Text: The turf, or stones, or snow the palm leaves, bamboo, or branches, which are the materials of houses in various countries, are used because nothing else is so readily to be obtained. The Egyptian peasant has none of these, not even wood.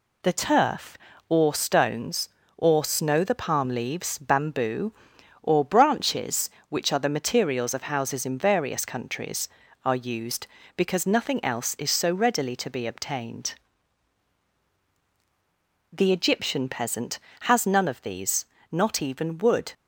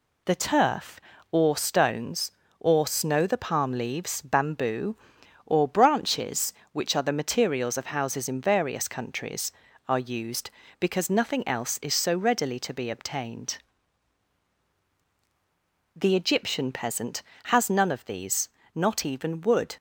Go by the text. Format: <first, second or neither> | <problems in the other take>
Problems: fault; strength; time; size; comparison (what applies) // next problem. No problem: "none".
neither | none